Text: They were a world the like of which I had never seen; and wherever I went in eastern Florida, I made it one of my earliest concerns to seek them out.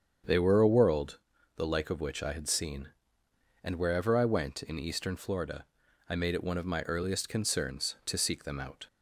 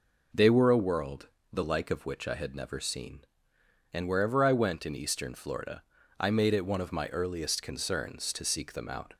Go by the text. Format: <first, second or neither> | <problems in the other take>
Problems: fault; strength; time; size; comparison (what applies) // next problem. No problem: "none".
second | starts louder than the rest; strong; until 1.6 s; 7.5 dB // pauses between "world" and "the"; at 1.1 s; 0.38 s long; slight in the second // skips "never"; at 2.4 s